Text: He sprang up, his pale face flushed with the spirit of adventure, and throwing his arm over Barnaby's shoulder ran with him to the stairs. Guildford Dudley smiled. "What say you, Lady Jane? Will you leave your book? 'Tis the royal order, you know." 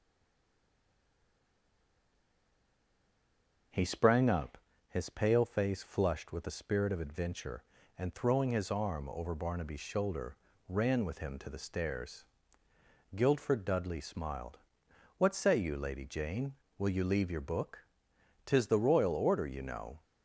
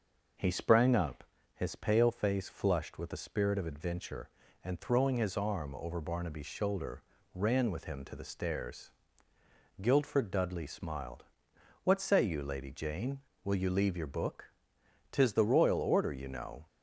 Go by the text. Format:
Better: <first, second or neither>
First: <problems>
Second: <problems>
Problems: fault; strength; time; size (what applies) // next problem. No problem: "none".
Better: second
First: stays silent before the first word; strong; until 3.7 s; 3.7 s long // pauses between "shoulder" and "ran"; slight; at 10.3 s; 0.32 s long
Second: pauses between "shoulder" and "ran"; slight; at 7.0 s; 0.32 s long